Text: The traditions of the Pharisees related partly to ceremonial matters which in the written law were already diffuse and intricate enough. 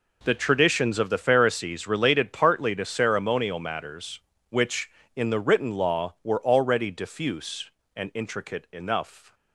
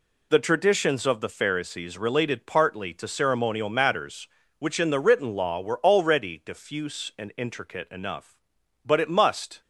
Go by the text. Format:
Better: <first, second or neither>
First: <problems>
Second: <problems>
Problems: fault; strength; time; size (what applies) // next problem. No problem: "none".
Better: first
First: none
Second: goes on to say "But it must"; noticeable; from 8.8 s on; 0.76 s long